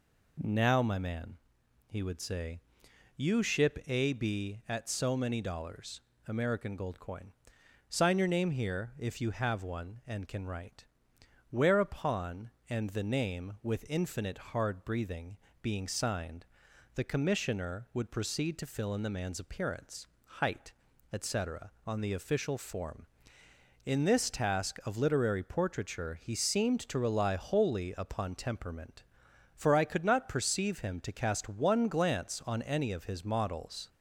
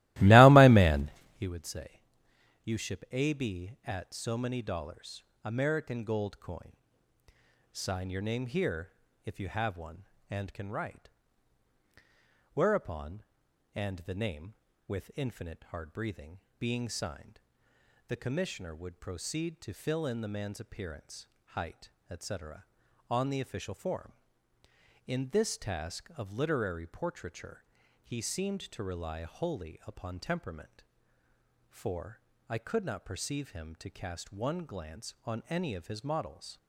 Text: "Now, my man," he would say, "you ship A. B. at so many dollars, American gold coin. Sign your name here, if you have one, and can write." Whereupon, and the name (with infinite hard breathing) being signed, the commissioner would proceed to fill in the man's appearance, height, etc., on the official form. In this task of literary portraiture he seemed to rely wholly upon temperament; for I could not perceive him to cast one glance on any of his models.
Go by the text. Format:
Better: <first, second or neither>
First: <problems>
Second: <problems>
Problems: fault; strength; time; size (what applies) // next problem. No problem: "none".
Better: first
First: none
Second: starts louder than the rest; strong; until 1.5 s; 17.5 dB // pauses between "portraiture" and "he"; at 27.6 s; 0.40 s long // pauses between "for" and "I"; slight; at 32.2 s; 0.28 s long